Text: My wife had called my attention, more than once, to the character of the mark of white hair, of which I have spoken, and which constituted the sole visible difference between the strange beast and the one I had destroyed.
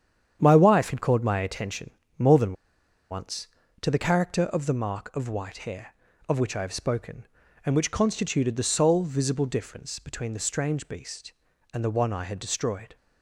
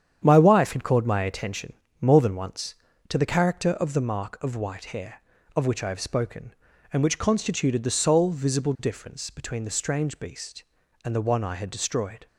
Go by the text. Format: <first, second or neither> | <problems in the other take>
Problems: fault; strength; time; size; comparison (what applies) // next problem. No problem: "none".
second | starts louder than the rest; strong; until 1.4 s; 9 dB; strong in the second // pauses between "than" and "once"; noticeable; at 2.5 s; 0.56 s long